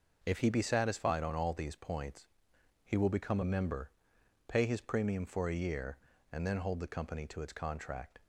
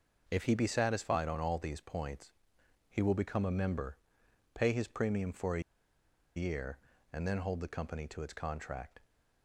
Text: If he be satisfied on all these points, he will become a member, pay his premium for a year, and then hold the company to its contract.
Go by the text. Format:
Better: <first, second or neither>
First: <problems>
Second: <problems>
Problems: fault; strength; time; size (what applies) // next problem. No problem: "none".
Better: first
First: none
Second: pauses between "a" and "year"; noticeable; at 5.6 s; 0.74 s long